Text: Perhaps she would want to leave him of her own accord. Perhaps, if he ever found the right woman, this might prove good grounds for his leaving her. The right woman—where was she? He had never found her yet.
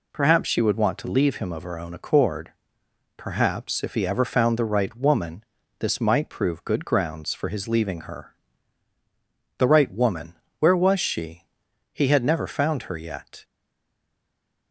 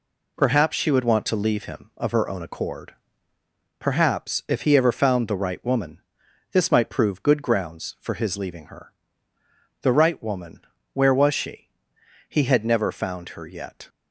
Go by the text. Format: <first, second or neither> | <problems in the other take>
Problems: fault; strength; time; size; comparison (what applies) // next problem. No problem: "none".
second | stays silent after the last word; noticeable; from 13.4 s on; 1.3 s long